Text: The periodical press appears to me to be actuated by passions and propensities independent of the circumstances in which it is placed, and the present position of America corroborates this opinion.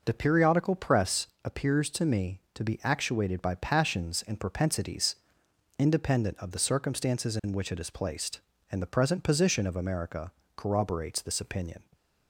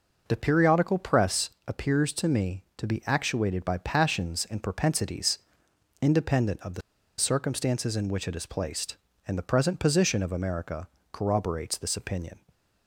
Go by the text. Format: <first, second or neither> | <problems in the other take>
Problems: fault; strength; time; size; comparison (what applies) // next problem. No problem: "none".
first | pauses between "press" and "appears"; slight; at 1.4 s; 0.18 s long; slight in the first // pauses between "propensities" and "independent"; noticeable; at 5.3 s; 0.64 s long; noticeable in the first // pauses between "the" and "circumstances"; at 6.8 s; 0.37 s long // pauses between "America" and "corroborates"; slight; at 10.8 s; 0.24 s long; slight in the first